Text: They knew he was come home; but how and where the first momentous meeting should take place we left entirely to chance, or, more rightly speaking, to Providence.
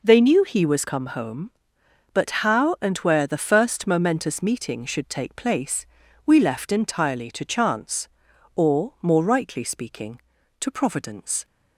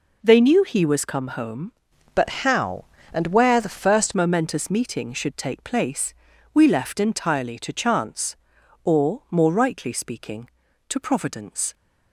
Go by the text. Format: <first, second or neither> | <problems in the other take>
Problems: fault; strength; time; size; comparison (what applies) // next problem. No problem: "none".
first | changes voice from "but" to "first"; from 2.1 to 4.1 s; 2.0 s long // pauses between "place" and "we"; at 6.1 s; 0.40 s long; also in the first